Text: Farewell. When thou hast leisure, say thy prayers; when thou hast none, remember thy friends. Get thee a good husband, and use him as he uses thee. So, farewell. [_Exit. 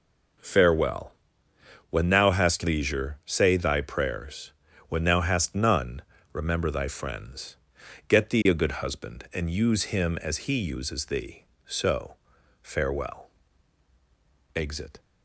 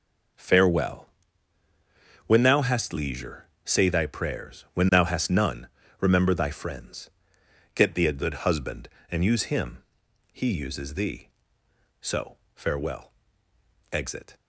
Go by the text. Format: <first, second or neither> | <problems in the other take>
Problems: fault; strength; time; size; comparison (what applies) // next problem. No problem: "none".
first | skips "as"; at 10.0 s